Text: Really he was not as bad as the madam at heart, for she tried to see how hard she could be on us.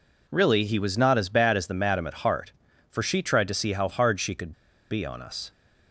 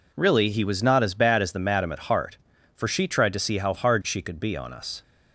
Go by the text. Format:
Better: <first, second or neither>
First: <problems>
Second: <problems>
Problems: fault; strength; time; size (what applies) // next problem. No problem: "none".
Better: second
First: pauses between "could" and "be"; at 4.5 s; 0.38 s long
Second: none